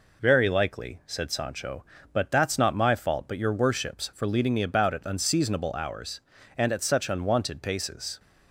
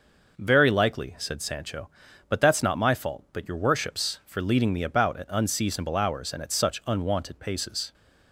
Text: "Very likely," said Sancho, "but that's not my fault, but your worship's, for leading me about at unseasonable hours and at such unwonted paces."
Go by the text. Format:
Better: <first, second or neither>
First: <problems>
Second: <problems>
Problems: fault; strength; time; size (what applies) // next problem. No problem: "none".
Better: neither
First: none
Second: none